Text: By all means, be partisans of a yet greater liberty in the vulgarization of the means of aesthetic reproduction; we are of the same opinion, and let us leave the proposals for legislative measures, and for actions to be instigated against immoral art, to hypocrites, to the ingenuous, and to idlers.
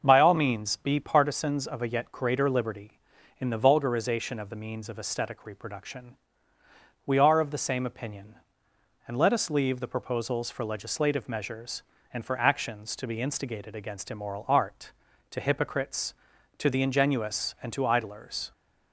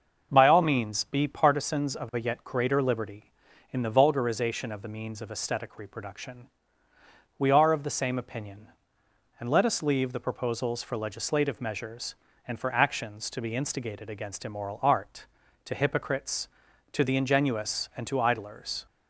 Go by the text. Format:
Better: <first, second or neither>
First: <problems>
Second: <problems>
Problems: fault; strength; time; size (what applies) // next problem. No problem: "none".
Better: neither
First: starts louder than the rest; until 1.0 s; 6.5 dB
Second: starts louder than the rest; until 1.3 s; 6.5 dB